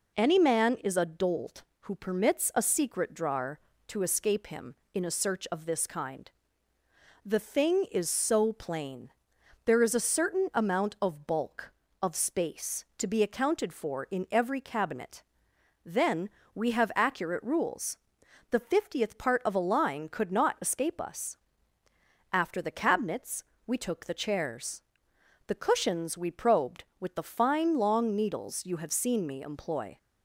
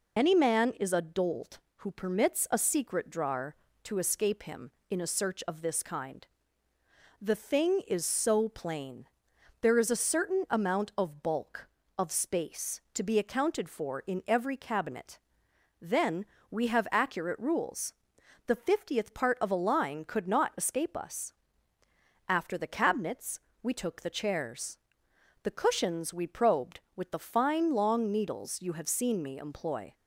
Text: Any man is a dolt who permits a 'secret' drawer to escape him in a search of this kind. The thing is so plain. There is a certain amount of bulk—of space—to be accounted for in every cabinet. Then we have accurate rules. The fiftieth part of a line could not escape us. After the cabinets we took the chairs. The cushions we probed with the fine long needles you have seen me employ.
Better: first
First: pauses between "Then" and "we"; slight; at 16.2 s; 0.24 s long // pauses between "cabinets" and "we"; slight; at 23.4 s; 0.24 s long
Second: loses the start of "Any"; at 0.1 s; 50 ms // pauses between "Then" and "we"; slight; at 16.2 s; 0.24 s long // pauses between "cabinets" and "we"; slight; at 23.3 s; 0.24 s long

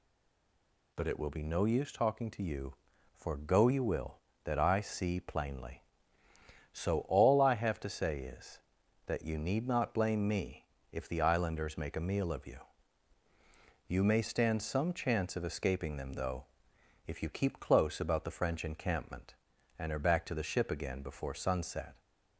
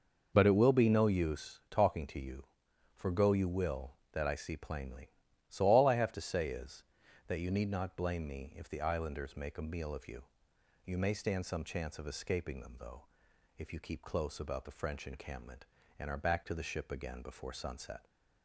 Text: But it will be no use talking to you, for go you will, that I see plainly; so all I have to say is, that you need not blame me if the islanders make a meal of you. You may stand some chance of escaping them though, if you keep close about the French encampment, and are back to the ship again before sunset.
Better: second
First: stays silent before the first word; slight; until 0.9 s; 0.9 s long // pauses between "me" and "if"; slight; at 10.6 s; 0.26 s long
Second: none

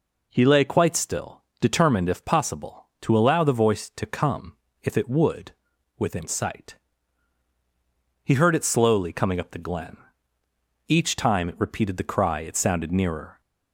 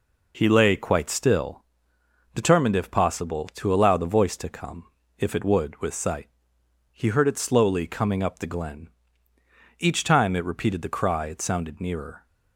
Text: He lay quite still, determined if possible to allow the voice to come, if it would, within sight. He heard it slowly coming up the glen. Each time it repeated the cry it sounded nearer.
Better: first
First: none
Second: says "with" for "within"; at 5.7 s

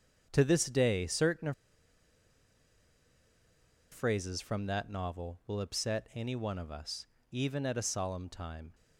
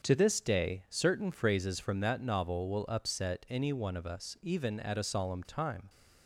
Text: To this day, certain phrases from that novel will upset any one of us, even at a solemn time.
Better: second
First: starts louder than the rest; strong; until 1.3 s; 8 dB // pauses between "certain" and "phrases"; strong; at 1.5 s; 2.4 s long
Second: starts louder than the rest; until 1.1 s; 7 dB

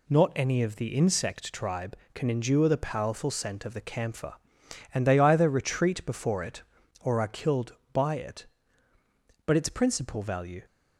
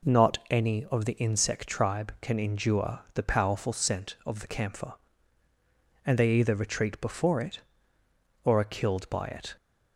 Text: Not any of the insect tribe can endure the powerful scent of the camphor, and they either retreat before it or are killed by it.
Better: second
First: goes on to say "But its principal value"; noticeable; from 9.4 s on; 1.1 s long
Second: none

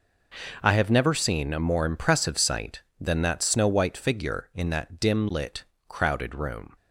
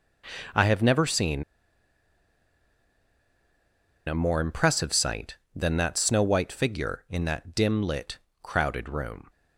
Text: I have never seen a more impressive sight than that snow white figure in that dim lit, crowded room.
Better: first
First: none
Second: pauses between "seen" and "a"; strong; at 1.4 s; 2.6 s long

